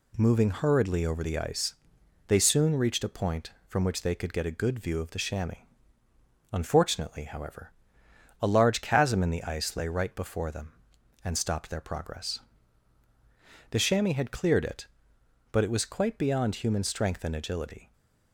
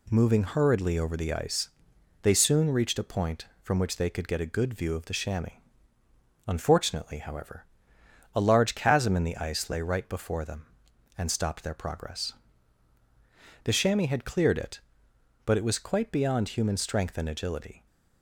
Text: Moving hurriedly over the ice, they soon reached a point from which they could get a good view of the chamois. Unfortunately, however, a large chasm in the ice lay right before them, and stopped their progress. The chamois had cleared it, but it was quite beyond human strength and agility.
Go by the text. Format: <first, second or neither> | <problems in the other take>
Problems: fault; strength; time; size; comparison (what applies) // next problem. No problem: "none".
neither | none